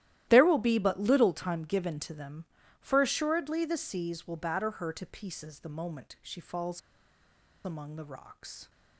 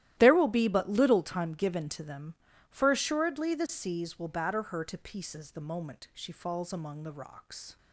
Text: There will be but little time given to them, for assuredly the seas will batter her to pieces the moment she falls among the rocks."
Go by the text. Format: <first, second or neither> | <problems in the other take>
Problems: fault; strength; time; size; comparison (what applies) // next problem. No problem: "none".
second | starts louder than the rest; strong; until 1.3 s; 14 dB; strong in the second // pauses between "falls" and "among"; noticeable; at 6.8 s; 0.85 s long